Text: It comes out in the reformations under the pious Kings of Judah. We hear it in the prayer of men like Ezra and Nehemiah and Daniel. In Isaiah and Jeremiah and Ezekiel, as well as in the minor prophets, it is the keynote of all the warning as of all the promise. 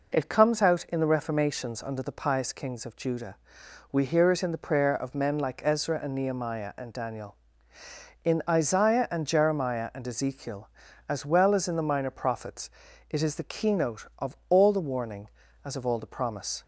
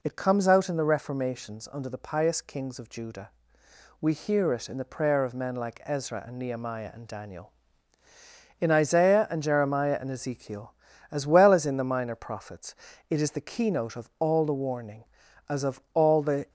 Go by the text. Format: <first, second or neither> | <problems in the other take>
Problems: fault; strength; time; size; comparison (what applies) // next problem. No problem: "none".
first | stops before "promise"; at 16.4 s